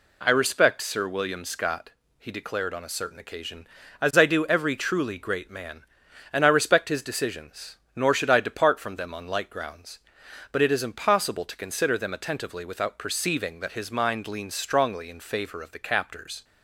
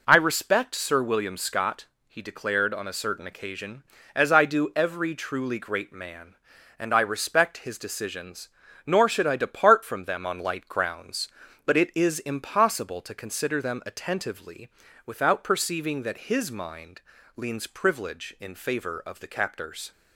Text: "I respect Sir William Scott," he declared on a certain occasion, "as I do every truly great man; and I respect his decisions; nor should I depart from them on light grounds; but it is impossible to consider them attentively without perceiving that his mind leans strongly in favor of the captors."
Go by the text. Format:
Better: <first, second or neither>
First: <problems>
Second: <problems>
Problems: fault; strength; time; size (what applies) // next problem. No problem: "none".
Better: first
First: none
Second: pauses between "attentively" and "without"; slight; at 14.6 s; 0.36 s long // pauses between "mind" and "leans"; slight; at 17.0 s; 0.34 s long // says "privilege" for "strongly"; at 17.6 s